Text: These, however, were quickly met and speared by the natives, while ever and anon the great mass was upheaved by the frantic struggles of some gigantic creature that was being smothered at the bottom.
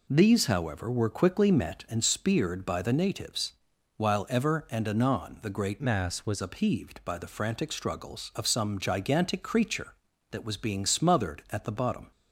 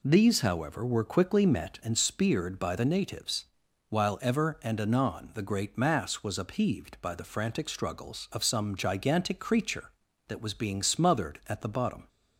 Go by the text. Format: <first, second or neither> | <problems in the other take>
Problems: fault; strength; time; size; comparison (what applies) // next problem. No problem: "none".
second | changes voice from "mass" to "was"; from 5.8 to 6.4 s; 0.6 s long